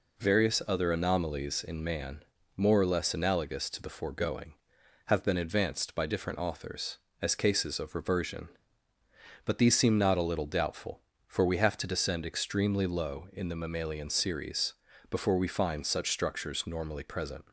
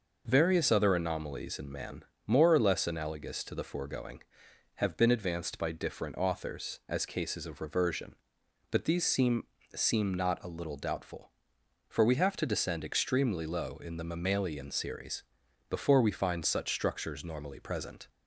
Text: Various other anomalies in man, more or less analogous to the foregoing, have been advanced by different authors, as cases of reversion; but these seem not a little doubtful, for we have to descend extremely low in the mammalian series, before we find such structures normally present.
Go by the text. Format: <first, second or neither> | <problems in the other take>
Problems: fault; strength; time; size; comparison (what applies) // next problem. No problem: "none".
first | says "seem" twice; at 9.7 s